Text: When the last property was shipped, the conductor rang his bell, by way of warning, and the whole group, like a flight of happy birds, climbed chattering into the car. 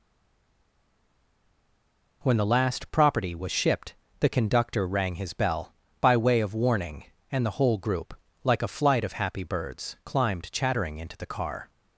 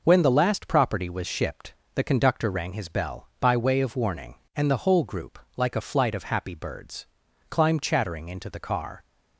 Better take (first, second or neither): second